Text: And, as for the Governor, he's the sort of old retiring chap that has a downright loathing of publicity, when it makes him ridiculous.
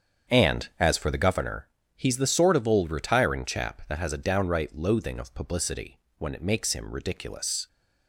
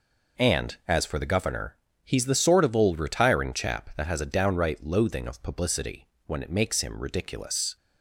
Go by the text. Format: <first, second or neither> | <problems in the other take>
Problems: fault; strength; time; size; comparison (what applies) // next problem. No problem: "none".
second | starts louder than the rest; strong; until 1.5 s; 7.5 dB